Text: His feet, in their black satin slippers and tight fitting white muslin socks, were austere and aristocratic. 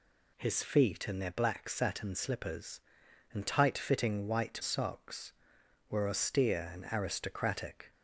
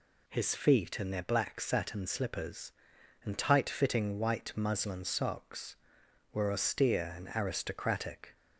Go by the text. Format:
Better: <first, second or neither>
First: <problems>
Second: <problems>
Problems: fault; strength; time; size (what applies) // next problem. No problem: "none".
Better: second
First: skips "muslin"; at 4.6 s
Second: none